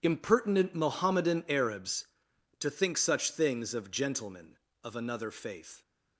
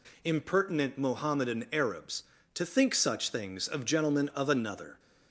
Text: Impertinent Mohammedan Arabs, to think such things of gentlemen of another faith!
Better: first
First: none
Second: stops before "faith"; at 4.9 s

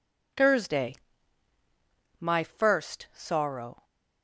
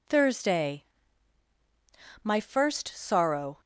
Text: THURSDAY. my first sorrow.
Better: neither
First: none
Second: none

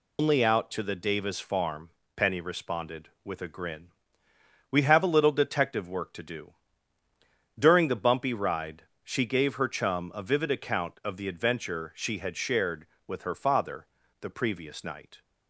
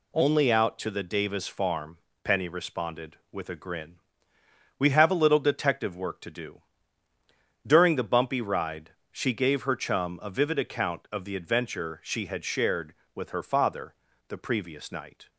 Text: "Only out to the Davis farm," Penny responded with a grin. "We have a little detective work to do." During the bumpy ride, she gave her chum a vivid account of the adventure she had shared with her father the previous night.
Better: second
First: loses the start of "Only"; at 0.1 s; 130 ms // pauses between "father" and "the"; slight; at 13.8 s; 0.34 s long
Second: pauses between "father" and "the"; slight; at 13.9 s; 0.34 s long

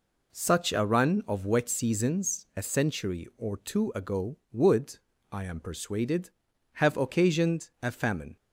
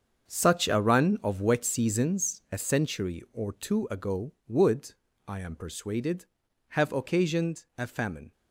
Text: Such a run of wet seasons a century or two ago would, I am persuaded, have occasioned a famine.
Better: first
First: none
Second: gets quieter; strong; throughout; 11.5 dB

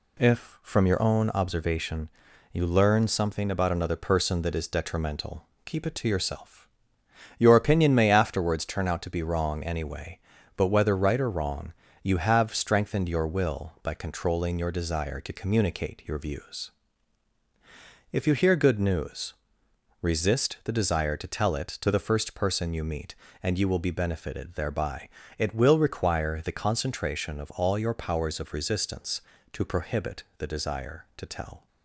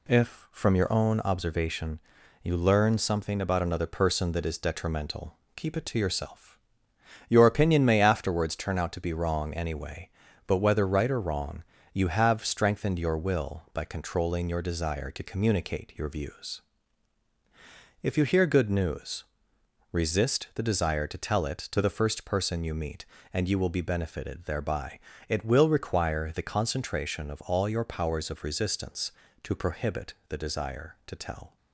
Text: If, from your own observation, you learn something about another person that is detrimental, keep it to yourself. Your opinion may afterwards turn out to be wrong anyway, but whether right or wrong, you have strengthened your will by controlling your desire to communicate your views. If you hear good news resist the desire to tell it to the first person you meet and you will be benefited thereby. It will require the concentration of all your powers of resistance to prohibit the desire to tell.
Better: neither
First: pauses between "news" and "resist"; noticeable; at 19.3 s; 0.70 s long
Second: pauses between "news" and "resist"; noticeable; at 19.2 s; 0.70 s long

